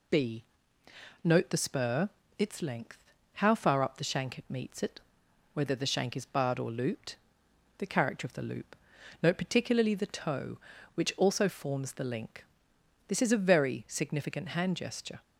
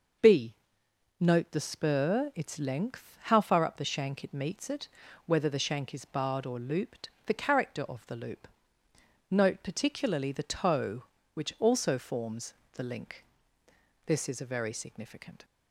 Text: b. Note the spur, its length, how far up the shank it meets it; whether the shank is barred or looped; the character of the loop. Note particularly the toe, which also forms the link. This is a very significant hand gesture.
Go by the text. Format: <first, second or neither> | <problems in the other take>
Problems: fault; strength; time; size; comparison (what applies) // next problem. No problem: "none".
first | pauses between "forms" and "the"; slight; at 12.5 s; 0.18 s long // stops before "hand gesture"; at 15.4 s